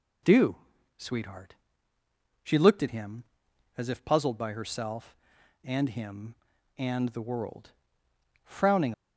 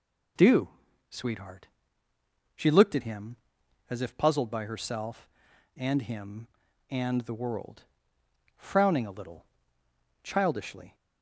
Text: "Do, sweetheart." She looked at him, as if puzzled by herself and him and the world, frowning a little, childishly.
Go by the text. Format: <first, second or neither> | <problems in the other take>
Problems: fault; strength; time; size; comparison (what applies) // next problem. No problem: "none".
second | stops before "a little childishly"; at 8.9 s